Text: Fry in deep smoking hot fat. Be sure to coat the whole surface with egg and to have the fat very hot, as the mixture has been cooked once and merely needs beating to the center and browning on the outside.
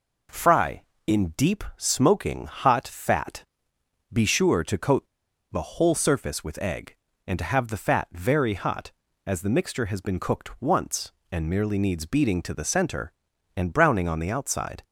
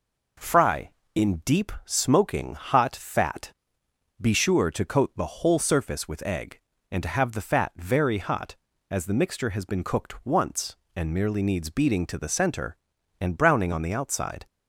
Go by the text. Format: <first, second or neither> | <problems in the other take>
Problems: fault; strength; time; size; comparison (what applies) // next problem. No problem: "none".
second | pauses between "coat" and "the"; noticeable; at 5.0 s; 0.47 s long